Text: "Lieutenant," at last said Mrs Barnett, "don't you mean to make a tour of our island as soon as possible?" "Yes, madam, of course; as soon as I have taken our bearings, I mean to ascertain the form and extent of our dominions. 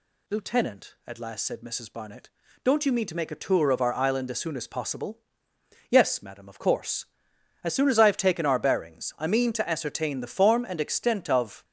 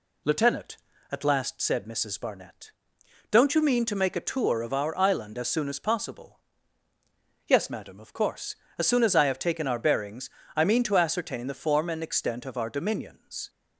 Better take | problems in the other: second | stops before "our dominions"; at 11.6 s

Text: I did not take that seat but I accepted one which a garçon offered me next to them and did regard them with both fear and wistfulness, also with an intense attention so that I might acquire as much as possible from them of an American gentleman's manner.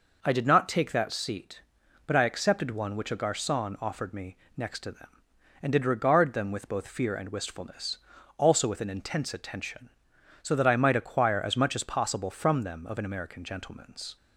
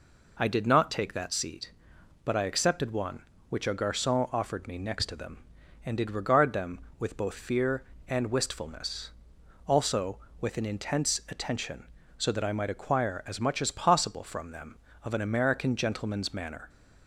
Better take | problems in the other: second | pauses between "me" and "next"; slight; at 4.3 s; 0.18 s long // stops before "manner"; at 14.1 s

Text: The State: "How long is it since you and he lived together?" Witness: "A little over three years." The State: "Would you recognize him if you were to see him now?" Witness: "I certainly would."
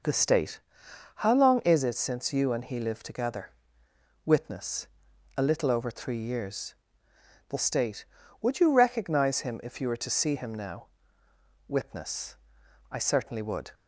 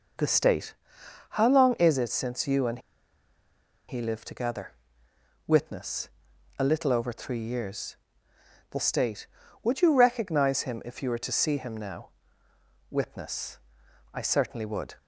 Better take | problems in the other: first | pauses between "and" and "he"; at 2.7 s; 1.1 s long

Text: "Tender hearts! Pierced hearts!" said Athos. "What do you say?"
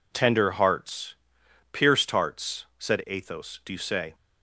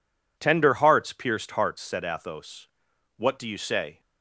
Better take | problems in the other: second | skips "What"; at 3.6 s

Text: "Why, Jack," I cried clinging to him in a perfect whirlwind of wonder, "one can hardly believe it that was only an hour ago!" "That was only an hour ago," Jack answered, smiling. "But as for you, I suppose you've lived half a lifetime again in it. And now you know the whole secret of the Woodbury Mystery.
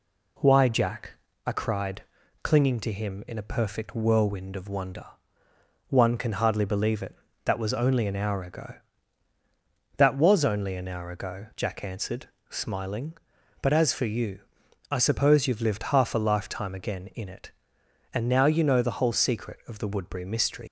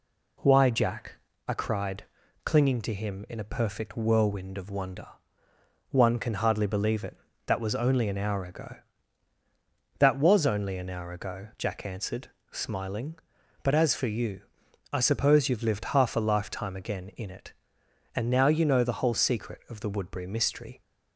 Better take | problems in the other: second | pauses between "cried" and "clinging"; at 2.0 s; 0.40 s long; also in the second // leaves "Mystery" unfinished; at 20.6 s; 115 ms

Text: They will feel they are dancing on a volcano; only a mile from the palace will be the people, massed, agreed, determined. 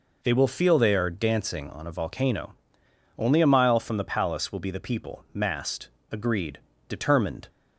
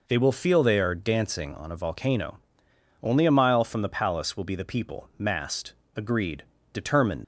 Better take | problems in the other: first | leaves "determined" unfinished; at 7.2 s; 85 ms

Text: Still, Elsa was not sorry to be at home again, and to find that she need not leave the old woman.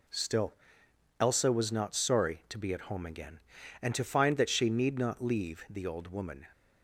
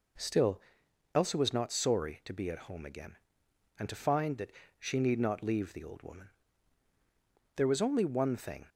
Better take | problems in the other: first | pauses between "that" and "she"; slight; at 4.5 s; 0.28 s long // goes on to say "There was only one thing"; noticeable; from 7.5 s on; 1.1 s long

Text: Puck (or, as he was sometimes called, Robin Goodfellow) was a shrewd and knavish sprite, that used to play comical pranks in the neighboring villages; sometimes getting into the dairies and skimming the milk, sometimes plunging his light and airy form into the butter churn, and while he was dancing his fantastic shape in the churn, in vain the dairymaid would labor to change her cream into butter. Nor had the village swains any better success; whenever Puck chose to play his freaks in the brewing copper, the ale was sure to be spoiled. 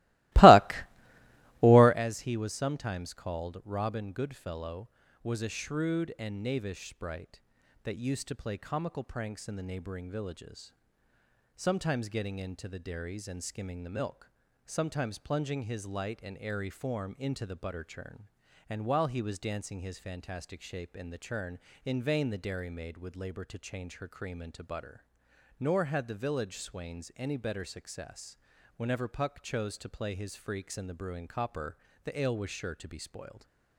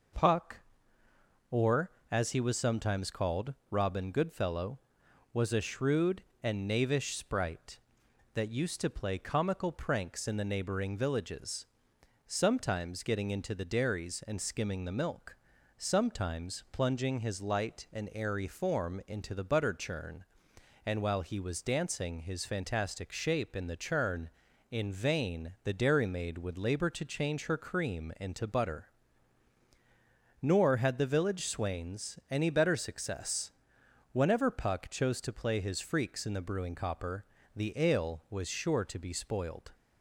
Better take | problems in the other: second | starts louder than the rest; strong; until 2.1 s; 20.5 dB

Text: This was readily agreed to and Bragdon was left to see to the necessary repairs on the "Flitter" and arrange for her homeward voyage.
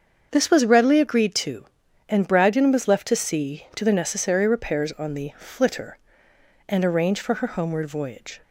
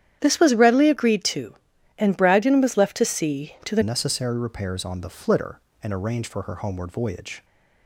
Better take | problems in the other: first | starts louder than the rest; strong; until 1.2 s; 10 dB; also in the first // changes voice at "necessary"; from 3.8 s on; 3.6 s long

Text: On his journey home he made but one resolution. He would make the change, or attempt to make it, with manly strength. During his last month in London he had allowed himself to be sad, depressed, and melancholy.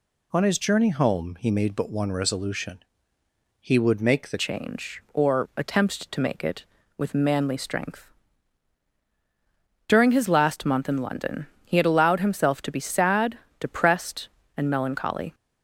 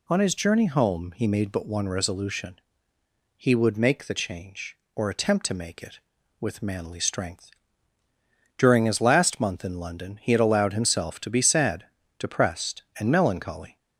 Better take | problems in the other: second | changes voice at "change"; from 4.3 s on; 11.0 s long // pauses between "London" and "he"; slight; at 11.4 s; 0.18 s long

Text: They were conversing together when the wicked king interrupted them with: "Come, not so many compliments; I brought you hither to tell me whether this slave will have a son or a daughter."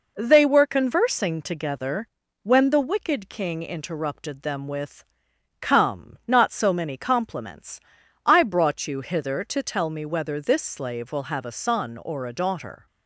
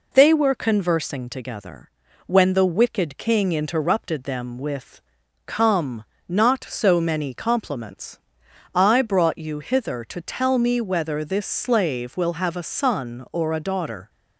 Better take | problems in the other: neither | pauses between "together" and "when"; the same in both

